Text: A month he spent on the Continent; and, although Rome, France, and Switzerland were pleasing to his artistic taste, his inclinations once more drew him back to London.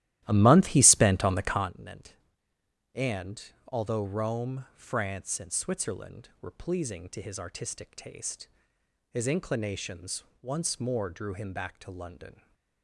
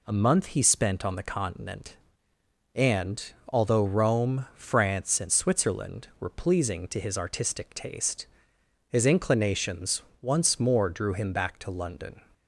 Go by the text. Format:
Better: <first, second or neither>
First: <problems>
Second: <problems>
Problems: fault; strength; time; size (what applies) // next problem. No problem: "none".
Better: second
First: starts louder than the rest; strong; until 1.7 s; 14 dB // pauses between "inclinations" and "once"; slight; at 10.2 s; 0.20 s long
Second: pauses between "inclinations" and "once"; slight; at 9.9 s; 0.22 s long